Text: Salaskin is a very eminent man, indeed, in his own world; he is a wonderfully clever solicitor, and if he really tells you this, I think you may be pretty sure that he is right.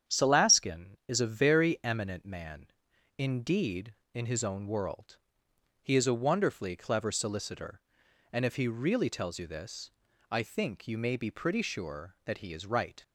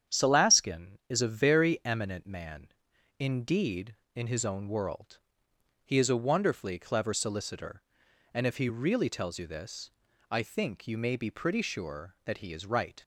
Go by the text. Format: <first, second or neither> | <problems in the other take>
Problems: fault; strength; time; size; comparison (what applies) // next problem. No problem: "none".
neither | starts louder than the rest; strong; the same in both